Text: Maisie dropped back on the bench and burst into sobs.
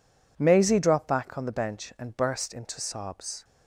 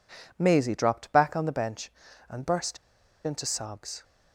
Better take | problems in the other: first | pauses between "burst" and "into"; noticeable; at 2.7 s; 0.49 s long

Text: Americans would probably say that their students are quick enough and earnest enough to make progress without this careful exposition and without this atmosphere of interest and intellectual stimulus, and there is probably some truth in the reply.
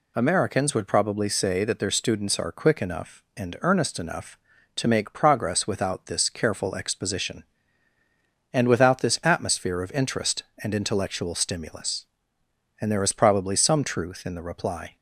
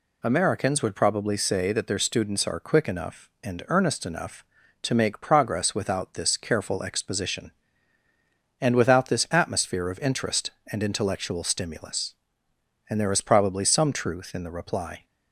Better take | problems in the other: neither | none

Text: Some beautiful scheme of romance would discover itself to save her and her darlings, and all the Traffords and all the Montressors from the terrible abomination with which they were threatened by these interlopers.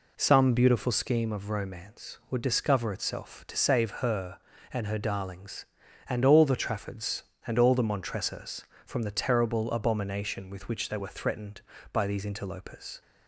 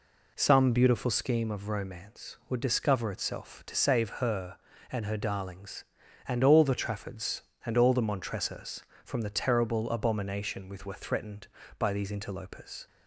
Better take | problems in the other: first | skips "which they"; at 10.8 s

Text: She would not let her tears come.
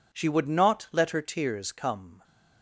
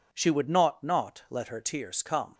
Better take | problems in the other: first | says "not" twice; at 0.8 s

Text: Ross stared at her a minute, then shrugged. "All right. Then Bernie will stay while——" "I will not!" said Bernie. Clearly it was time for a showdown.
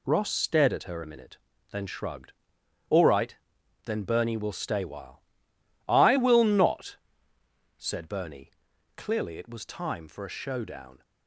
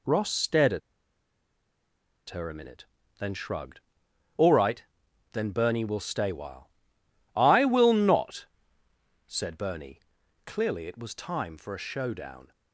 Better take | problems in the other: first | pauses between "at" and "her"; strong; at 0.8 s; 1.5 s long

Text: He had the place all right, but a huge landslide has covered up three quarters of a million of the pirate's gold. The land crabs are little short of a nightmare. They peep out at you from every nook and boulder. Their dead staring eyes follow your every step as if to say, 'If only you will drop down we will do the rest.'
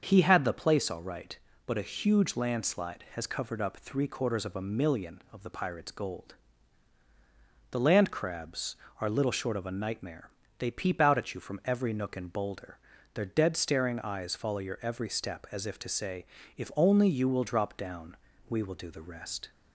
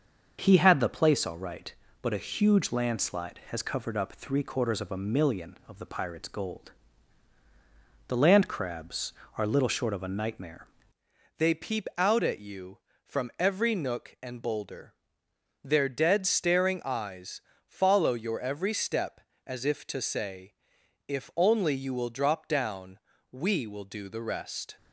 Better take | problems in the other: first | starts louder than the rest; until 1.4 s; 6.5 dB; also in the first // changes voice at "They"; from 11.3 s on; 13.4 s long // pauses between "eyes" and "follow"; slight; at 17.4 s; 0.26 s long // pauses between "down" and "we"; slight; at 22.9 s; 0.32 s long; slight in the first

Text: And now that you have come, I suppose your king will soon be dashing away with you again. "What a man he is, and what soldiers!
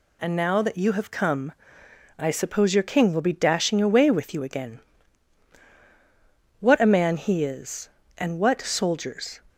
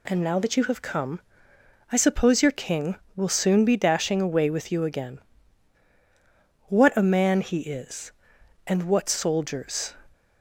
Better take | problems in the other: second | skips "soon"; at 3.2 s

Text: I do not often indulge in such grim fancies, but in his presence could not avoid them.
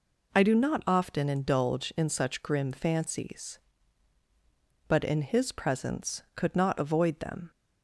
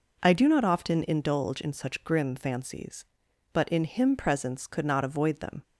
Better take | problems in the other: first | says "him" for "his"; at 3.8 s

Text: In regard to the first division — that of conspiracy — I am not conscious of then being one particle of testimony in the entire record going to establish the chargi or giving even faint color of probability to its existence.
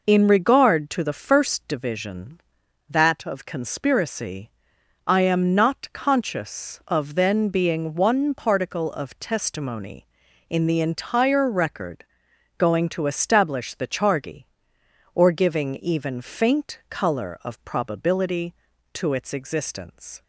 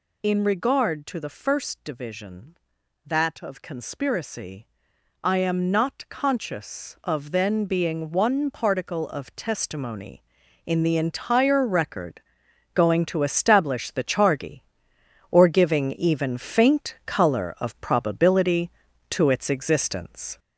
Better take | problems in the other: first | gets louder; noticeable; throughout; 5 dB // pauses between "record" and "going"; noticeable; at 12.1 s; 0.56 s long; noticeable in the first

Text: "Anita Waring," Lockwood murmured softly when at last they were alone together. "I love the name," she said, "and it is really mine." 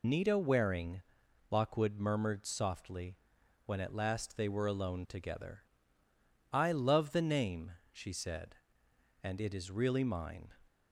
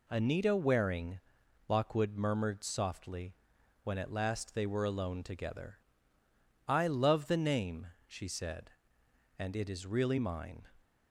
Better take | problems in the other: second | loses the start of "Anita"; at 0.0 s; 135 ms // pauses between "softly" and "when"; noticeable; at 3.1 s; 0.48 s long; noticeable in the second

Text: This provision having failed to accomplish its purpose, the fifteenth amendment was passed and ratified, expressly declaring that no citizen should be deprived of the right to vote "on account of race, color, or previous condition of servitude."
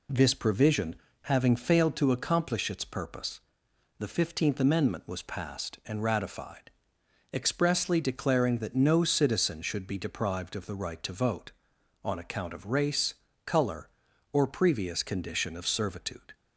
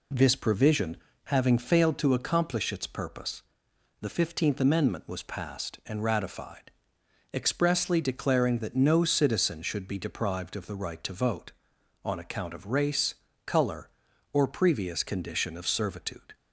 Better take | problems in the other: neither | pauses between "provision" and "having"; slight; the same in both

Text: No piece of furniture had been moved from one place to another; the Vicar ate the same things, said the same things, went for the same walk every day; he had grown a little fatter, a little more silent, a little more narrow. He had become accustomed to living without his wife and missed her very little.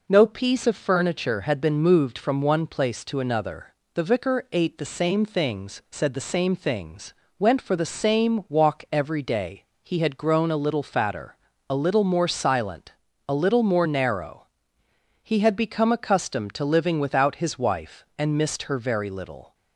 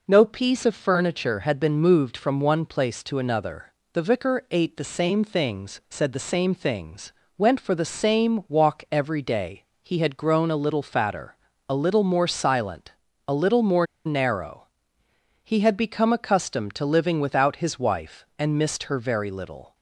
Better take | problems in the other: first | pauses between "more" and "narrow"; slight; at 13.8 s; 0.20 s long

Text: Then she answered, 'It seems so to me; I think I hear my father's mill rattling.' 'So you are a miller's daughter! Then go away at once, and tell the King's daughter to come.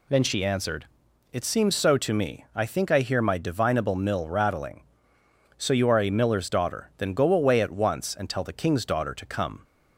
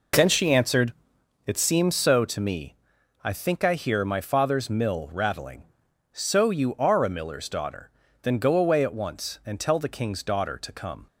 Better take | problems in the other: second | says "divinable" for "father's"; at 3.3 s

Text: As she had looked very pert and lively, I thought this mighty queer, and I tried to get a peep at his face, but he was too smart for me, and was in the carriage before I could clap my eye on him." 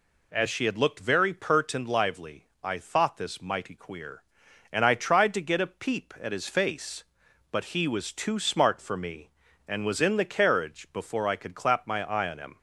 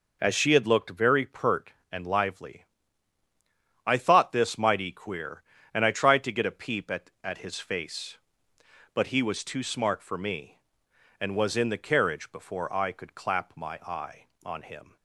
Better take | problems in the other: first | says "at" twice; at 7.2 s

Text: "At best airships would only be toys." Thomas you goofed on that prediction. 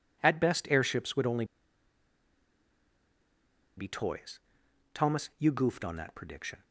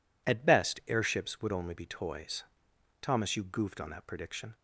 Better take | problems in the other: second | pauses between "only" and "be"; strong; at 1.4 s; 2.3 s long

